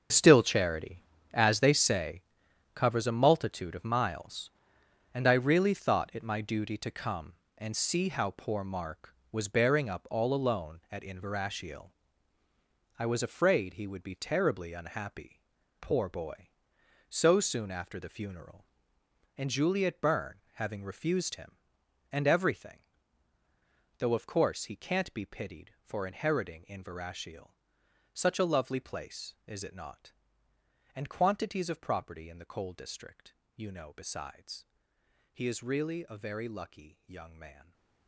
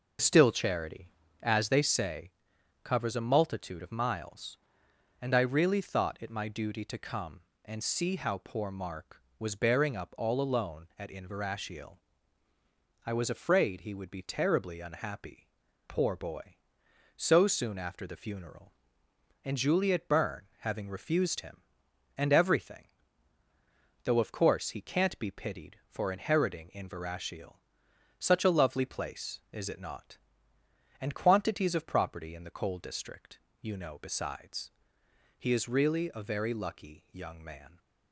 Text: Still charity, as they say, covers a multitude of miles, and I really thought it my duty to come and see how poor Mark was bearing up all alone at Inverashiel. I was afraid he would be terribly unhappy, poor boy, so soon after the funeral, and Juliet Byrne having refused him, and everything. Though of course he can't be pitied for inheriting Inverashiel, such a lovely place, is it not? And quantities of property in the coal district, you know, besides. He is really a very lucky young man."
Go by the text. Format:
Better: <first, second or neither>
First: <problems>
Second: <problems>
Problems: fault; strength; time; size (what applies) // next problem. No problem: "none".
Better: second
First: gets quieter; strong; throughout; 12.5 dB // stays silent after the last word; slight; from 37.5 s on; 0.5 s long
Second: none